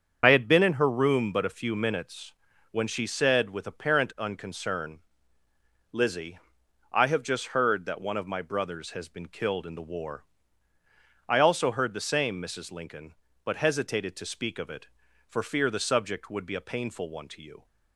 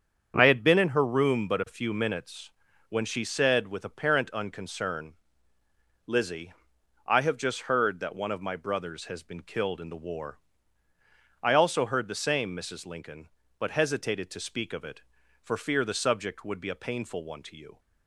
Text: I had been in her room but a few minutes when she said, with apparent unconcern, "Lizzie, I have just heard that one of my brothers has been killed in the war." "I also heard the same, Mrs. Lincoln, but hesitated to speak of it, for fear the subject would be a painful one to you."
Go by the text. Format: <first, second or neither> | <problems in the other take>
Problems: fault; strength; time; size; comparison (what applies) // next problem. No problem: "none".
second | loses the start of "I"; at 0.2 s; 50 ms // starts louder than the rest; strong; until 1.2 s; 7.5 dB; strong in the second // pauses between "minutes" and "when"; at 2.3 s; 0.38 s long; also in the second